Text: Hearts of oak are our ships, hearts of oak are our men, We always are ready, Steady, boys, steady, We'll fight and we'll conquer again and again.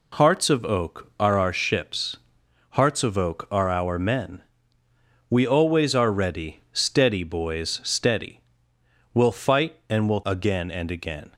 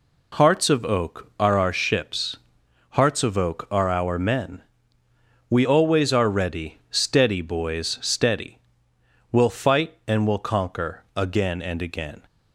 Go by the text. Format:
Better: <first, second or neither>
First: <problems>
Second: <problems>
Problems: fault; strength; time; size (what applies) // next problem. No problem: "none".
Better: second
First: skips "conquer"; at 10.2 s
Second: none